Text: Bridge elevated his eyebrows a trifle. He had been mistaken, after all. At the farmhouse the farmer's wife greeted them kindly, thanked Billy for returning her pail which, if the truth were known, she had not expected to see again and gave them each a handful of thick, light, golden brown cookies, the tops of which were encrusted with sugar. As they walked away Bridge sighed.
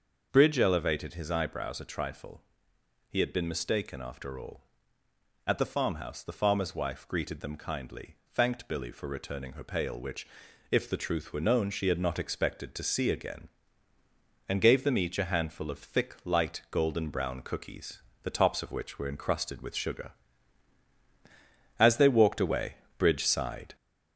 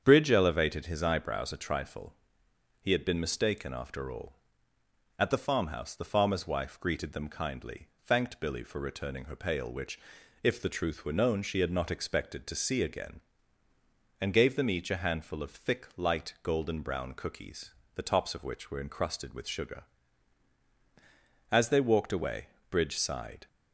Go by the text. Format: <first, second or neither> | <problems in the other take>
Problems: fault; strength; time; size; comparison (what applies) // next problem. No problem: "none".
second | gets louder; slight; throughout; 3 dB // starts louder than the rest; noticeable; until 1.3 s; 6 dB; strong in the second // pauses between "away" and "Bridge"; slight; at 22.7 s; 0.24 s long; slight in the second